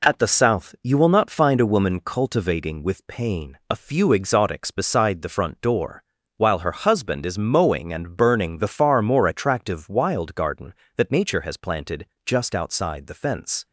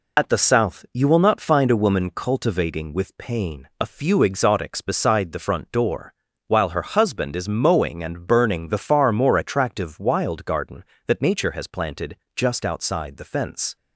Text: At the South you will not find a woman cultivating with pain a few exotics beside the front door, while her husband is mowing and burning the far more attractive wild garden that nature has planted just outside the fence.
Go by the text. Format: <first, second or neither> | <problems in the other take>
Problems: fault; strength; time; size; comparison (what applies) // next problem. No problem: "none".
first | loses the start of "At"; at 0.1 s; 45 ms // pauses between "planted" and "just"; slight; at 12.1 s; 0.20 s long; slight in the first